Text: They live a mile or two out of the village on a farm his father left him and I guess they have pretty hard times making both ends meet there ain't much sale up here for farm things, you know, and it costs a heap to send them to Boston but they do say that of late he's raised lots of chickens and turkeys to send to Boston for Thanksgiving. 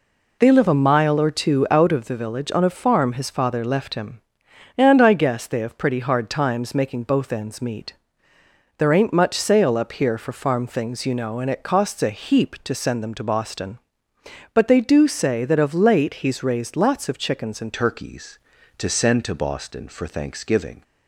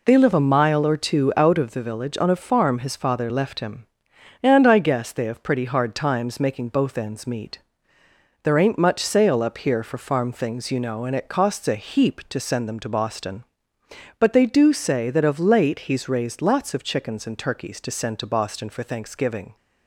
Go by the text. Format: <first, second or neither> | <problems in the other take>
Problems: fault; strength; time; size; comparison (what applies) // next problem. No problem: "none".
second | pauses between "meet" and "there"; noticeable; at 7.9 s; 0.84 s long; noticeable in the second // changes voice at "turkeys"; from 17.7 s on; 3.1 s long